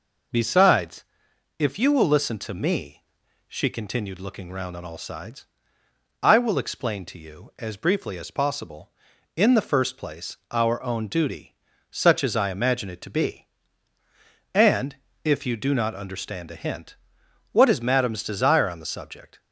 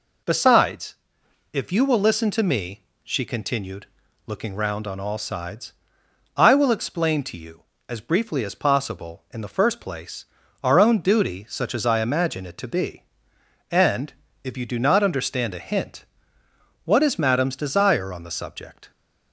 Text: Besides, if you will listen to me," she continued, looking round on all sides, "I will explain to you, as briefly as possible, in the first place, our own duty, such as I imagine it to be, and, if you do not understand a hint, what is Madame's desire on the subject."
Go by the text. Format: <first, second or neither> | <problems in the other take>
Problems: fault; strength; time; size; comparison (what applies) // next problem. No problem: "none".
neither | none